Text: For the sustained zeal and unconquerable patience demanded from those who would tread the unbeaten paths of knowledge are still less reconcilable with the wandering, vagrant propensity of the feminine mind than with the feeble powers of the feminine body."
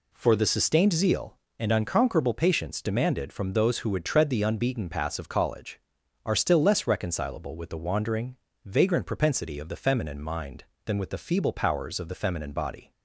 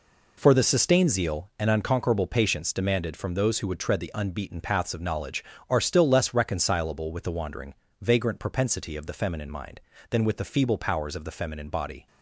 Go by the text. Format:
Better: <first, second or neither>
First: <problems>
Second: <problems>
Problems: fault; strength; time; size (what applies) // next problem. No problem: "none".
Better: second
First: says "college" for "knowledge"; at 5.2 s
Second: none